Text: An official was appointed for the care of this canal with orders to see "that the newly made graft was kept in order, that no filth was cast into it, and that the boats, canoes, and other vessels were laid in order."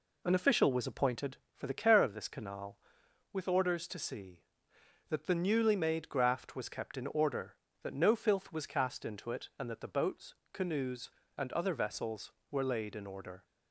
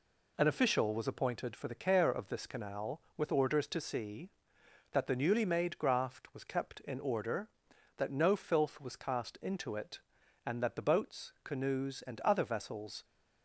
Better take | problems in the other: first | stops before "were laid in order"; at 13.0 s

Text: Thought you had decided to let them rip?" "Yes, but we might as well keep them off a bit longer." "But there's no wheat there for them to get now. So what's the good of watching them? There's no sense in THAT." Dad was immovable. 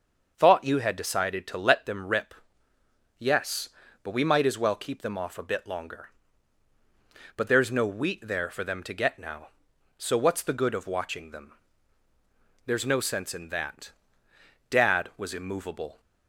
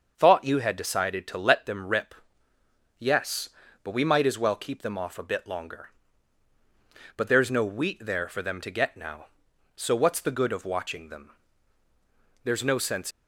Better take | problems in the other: first | starts louder than the rest; until 1.1 s; 6.5 dB; also in the first // stops before "in THAT Dad was immovable"; at 13.1 s

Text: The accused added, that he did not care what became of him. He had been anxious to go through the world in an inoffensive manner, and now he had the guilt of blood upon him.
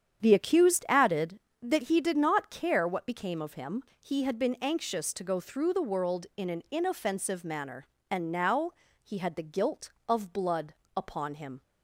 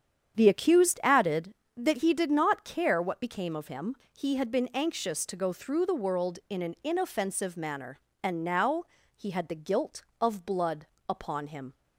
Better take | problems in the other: neither | starts louder than the rest; strong; the same in both // pauses between "now" and "he"; slight; the same in both // pauses between "blood" and "upon"; slight; the same in both

